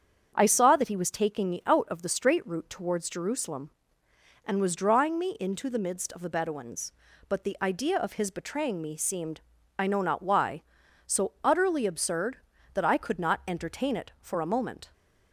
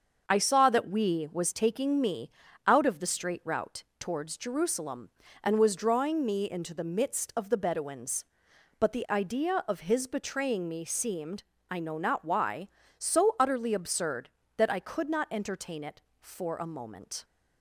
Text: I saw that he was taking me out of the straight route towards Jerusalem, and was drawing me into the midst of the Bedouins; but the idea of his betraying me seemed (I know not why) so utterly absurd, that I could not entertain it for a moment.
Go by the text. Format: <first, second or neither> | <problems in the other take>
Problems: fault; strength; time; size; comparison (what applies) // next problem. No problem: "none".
first | starts louder than the rest; until 1.3 s; 6.5 dB; strong in the first // says "we" for "he"; at 0.8 s // pauses between "me" and "out"; slight; at 2.3 s; 0.34 s long // pauses between "route" and "towards"; slight; at 3.8 s; 0.16 s long